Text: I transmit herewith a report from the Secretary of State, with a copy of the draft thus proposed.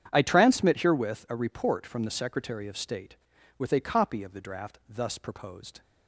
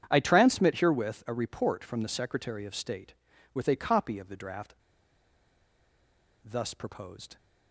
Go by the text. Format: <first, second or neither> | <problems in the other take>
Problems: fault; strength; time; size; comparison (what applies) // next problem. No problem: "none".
first | starts louder than the rest; strong; until 1.1 s; 8.5 dB; strong in the first // pauses between "draft" and "thus"; strong; at 4.7 s; 1.7 s long